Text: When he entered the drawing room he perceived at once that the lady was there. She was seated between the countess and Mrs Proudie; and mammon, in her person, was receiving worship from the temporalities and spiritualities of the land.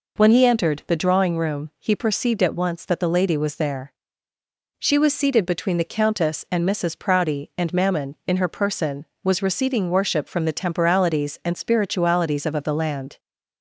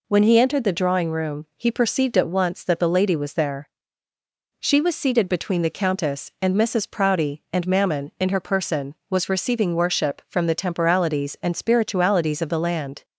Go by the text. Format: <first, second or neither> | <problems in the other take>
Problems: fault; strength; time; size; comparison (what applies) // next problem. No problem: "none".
second | says "of" twice; at 12.5 s